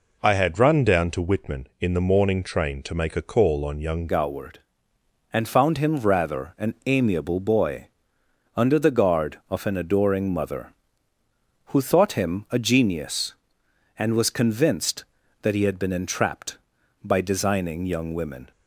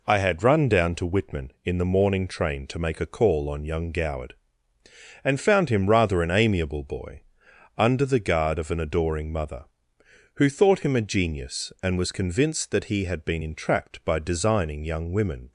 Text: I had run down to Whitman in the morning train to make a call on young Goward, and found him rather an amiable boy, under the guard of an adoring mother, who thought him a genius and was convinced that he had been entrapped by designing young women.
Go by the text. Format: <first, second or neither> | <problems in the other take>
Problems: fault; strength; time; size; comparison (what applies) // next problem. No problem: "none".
second | changes voice at "Goward"; from 4.0 s on; 14.5 s long